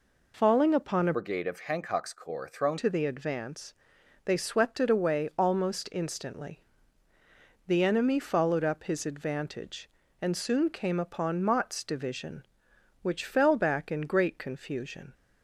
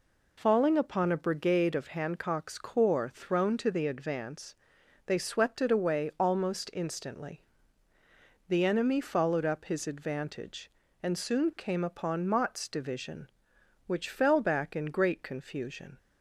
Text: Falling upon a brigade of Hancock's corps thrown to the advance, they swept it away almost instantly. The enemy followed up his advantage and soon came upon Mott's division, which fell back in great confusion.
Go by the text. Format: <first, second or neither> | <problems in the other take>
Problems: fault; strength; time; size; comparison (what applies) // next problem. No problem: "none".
second | changes voice from "brigade" to "thrown"; from 1.1 to 2.7 s; 1.6 s long